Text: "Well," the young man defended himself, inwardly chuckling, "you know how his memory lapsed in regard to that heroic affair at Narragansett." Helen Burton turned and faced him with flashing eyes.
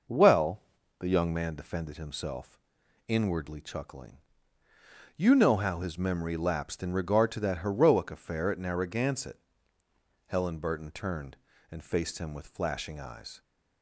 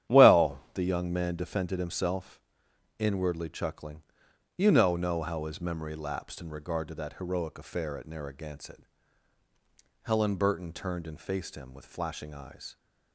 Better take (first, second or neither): first